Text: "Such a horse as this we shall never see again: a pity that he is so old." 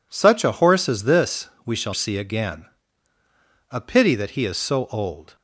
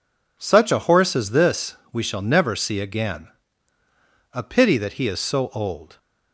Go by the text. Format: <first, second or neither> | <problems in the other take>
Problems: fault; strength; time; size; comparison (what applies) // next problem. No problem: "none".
second | pauses between "this" and "we"; slight; at 1.5 s; 0.16 s long; slight in the second // skips "never"; at 1.9 s